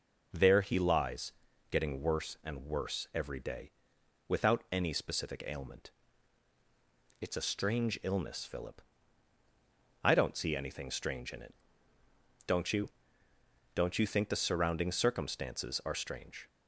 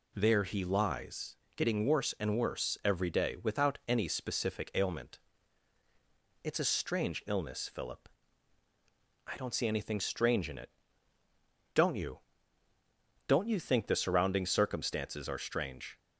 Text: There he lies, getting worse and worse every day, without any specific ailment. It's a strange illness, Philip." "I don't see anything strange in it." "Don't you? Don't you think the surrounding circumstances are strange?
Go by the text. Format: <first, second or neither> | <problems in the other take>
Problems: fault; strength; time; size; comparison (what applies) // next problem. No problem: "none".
neither | none